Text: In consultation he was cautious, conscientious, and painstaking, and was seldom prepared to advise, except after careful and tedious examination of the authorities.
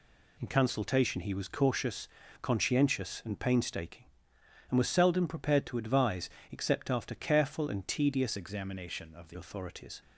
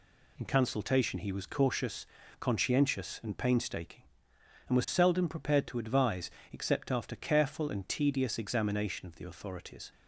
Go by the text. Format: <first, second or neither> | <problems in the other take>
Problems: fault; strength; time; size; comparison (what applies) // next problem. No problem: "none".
second | changes voice from "examination" to "the"; from 8.3 to 9.3 s; 1.0 s long